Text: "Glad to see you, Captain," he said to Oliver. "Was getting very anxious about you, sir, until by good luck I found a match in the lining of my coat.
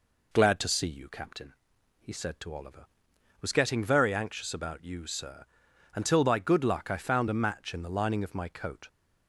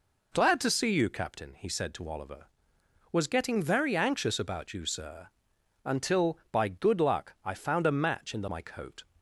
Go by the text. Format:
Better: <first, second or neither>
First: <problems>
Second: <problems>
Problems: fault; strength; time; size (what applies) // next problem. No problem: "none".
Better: first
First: none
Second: skips "lining of"; at 8.4 s